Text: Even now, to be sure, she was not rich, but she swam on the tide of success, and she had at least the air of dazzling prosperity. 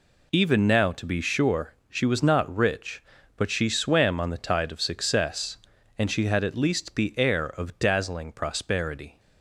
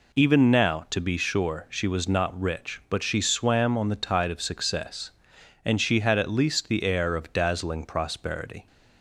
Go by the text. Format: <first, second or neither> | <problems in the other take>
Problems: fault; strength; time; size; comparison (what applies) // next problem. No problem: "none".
neither | none